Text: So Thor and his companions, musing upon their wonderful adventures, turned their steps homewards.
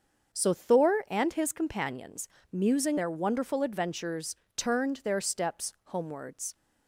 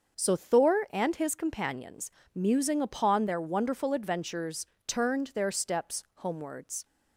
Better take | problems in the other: second | starts louder than the rest; until 1.4 s; 7 dB; also in the second // skips "upon"; at 2.9 s

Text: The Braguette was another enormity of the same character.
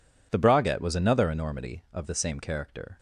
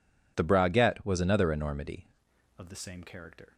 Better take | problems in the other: first | changes voice at "of"; from 2.5 s on; 1.0 s long

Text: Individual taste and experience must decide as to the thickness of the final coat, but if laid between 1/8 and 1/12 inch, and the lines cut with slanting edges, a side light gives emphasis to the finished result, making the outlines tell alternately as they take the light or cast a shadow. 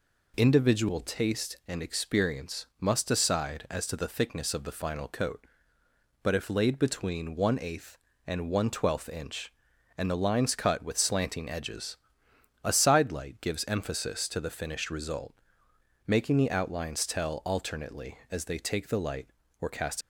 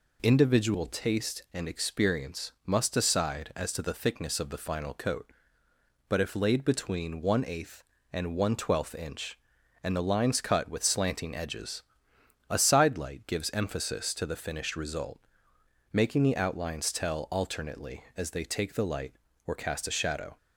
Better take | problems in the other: second | stops before "a shadow"; at 20.0 s

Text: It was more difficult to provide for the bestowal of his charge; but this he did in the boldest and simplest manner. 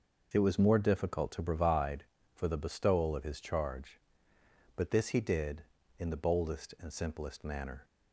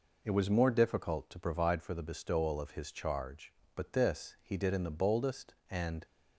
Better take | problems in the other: first | stops before "simplest manner"; at 6.0 s

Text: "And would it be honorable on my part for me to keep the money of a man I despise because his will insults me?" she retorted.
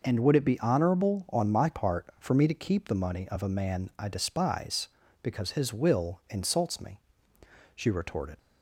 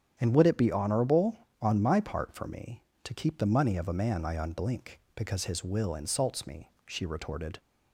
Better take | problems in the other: first | starts louder than the rest; strong; until 1.1 s; 8 dB // says "unblink" for "despise"; at 4.3 s

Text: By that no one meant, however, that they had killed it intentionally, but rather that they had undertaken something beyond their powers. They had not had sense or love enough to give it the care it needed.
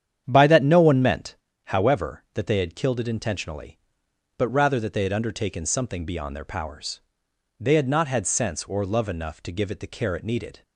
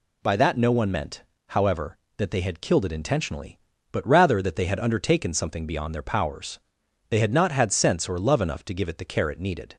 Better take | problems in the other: second | starts louder than the rest; strong; until 1.4 s; 9 dB

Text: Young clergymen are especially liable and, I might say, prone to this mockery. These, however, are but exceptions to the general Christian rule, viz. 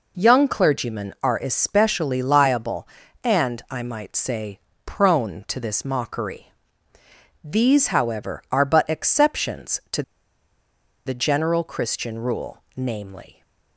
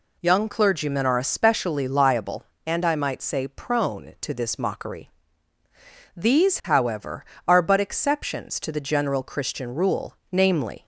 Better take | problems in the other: second | pauses between "to" and "the"; at 10.0 s; 1.0 s long

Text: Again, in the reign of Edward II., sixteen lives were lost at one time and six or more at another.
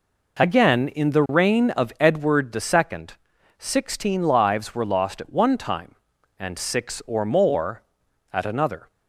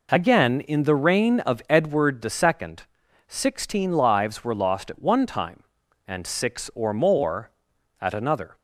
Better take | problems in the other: neither | none

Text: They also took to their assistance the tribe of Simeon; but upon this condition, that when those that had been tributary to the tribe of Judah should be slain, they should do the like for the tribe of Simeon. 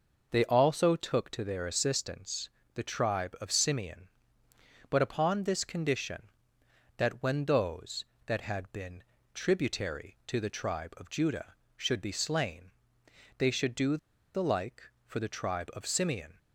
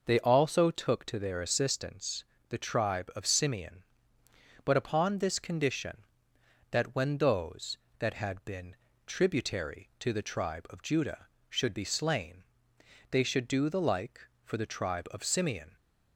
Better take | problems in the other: second | pauses between "assistance" and "the"; slight; at 2.4 s; 0.26 s long; slight in the second // pauses between "been" and "tributary"; slight; at 9.0 s; 0.30 s long; slight in the second // pauses between "do" and "the"; at 13.9 s; 0.37 s long

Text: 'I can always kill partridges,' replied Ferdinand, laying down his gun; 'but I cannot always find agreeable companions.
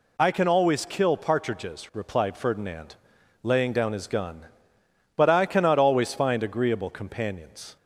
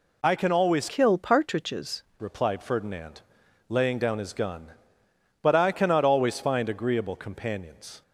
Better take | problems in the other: first | changes voice from "kill" to "partridges"; from 0.8 to 2.0 s; 1.2 s long

